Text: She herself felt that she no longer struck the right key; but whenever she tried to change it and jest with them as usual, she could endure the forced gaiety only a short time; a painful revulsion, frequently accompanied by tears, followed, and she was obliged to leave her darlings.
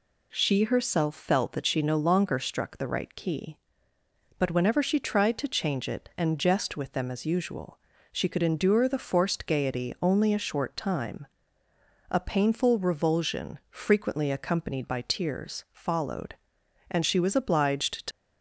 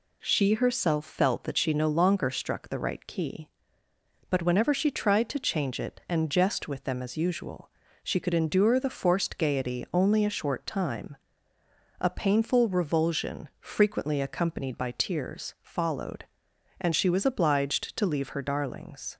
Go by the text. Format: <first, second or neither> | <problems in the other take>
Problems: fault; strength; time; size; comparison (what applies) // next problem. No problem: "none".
second | stops before "leave her darlings"; at 18.1 s